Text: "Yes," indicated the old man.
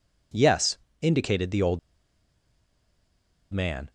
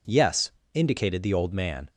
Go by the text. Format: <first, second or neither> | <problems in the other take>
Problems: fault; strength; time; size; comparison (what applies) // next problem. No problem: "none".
second | pauses between "old" and "man"; strong; at 1.7 s; 1.7 s long